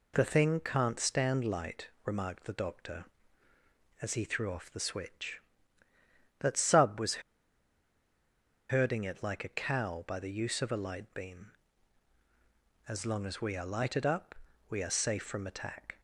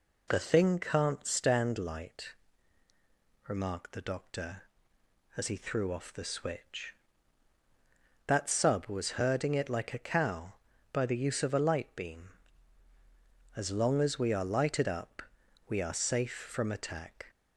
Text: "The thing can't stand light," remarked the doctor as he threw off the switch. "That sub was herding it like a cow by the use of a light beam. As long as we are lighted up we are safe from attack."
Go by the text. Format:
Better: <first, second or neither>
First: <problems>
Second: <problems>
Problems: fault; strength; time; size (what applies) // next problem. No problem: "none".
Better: second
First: pauses between "was" and "herding"; strong; at 7.2 s; 1.5 s long // pauses between "up" and "we"; slight; at 14.3 s; 0.36 s long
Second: pauses between "up" and "we"; noticeable; at 15.2 s; 0.46 s long